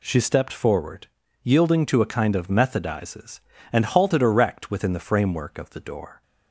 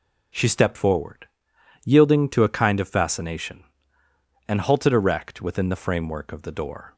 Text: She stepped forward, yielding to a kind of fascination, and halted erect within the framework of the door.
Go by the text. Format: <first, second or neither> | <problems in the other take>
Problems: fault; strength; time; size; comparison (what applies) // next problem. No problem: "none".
second | says "methodizes" for "fascination"; at 2.4 s